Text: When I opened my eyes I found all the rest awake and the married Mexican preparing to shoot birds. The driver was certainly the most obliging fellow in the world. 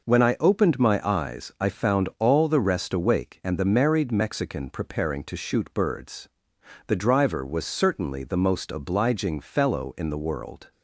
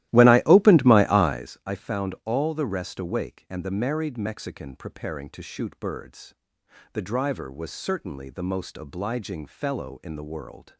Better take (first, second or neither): first